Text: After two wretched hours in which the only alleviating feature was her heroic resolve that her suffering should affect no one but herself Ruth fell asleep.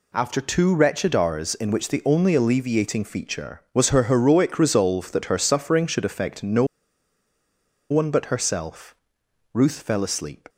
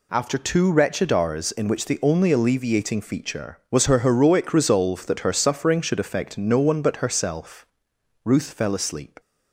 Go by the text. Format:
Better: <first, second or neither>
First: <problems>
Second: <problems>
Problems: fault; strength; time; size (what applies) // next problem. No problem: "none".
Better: second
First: pauses between "no" and "one"; strong; at 6.6 s; 1.2 s long // pauses between "herself" and "Ruth"; noticeable; at 8.9 s; 0.58 s long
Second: pauses between "herself" and "Ruth"; noticeable; at 7.6 s; 0.58 s long